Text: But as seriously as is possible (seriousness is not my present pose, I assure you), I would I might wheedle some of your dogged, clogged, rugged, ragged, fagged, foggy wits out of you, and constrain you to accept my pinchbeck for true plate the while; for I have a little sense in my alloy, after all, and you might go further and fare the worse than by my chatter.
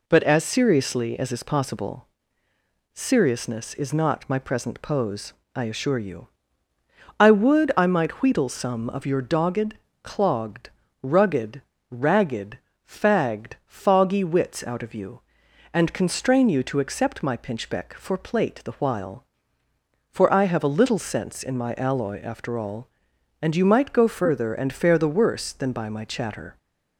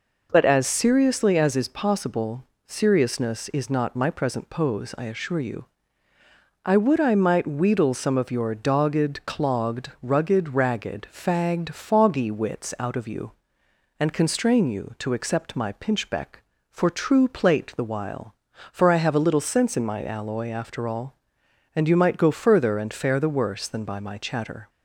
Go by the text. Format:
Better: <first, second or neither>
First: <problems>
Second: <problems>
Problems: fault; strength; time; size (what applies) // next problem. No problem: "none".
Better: second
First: skips "true"; at 18.1 s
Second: none